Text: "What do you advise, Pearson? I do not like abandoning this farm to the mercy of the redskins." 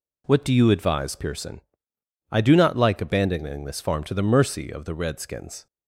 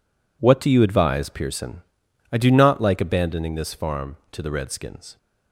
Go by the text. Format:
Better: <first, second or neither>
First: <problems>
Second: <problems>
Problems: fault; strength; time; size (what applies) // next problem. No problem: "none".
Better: first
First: none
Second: skips "the mercy of"; at 4.4 s